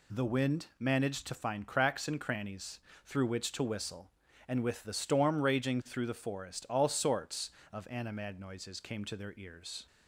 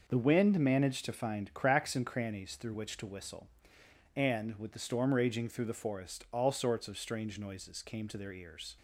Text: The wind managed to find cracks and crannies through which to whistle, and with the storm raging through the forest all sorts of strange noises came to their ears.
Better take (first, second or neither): second